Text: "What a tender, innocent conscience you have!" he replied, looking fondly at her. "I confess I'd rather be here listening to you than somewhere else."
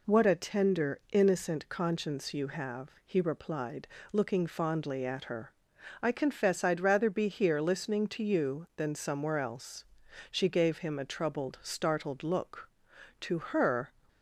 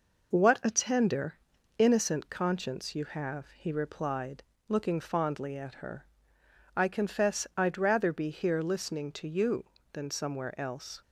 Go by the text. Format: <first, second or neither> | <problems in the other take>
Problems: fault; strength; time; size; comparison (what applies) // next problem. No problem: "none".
second | goes on to say "She gave him a troubled startled look To her"; strong; from 10.2 s on; 3.6 s long